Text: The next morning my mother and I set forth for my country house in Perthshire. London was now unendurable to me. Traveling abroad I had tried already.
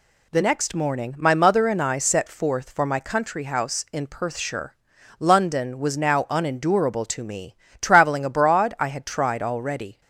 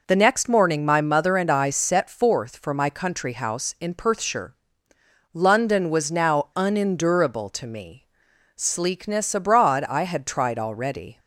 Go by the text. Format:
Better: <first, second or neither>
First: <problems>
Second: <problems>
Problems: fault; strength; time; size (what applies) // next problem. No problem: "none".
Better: first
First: none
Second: says "Sleekness" for "Traveling"; at 8.5 s